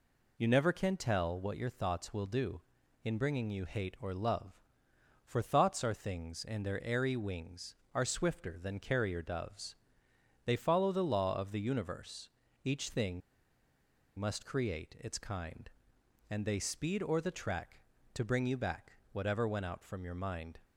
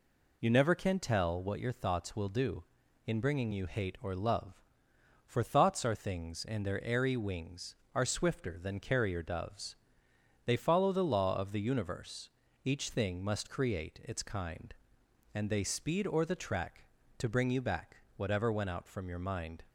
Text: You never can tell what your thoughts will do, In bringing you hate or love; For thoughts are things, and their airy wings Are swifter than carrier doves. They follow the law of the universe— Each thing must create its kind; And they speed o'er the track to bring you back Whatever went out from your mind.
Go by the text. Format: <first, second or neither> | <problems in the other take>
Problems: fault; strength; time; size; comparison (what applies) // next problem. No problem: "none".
second | pauses between "thing" and "must"; noticeable; at 13.2 s; 0.97 s long // pauses between "back" and "Whatever"; slight; at 18.9 s; 0.20 s long; slight in the second